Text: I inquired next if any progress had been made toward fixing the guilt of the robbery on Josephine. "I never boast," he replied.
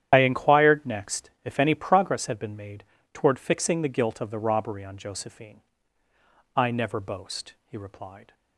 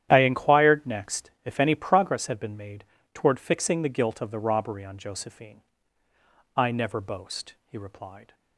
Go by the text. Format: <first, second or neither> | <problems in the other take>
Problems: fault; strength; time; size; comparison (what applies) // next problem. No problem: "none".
second | loses the start of "I"; at 0.1 s; 35 ms // starts louder than the rest; strong; until 1.1 s; 10.5 dB; strong in the second // pauses between "made" and "toward"; slight; at 2.8 s; 0.30 s long; slight in the second